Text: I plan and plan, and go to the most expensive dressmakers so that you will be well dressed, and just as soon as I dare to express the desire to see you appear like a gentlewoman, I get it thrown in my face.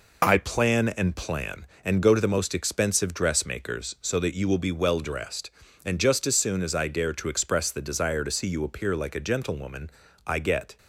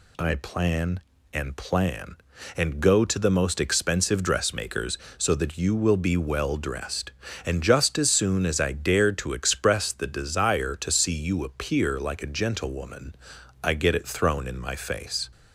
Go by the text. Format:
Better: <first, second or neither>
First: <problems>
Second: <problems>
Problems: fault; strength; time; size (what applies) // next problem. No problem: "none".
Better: second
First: stops before "it thrown in my face"; at 10.7 s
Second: none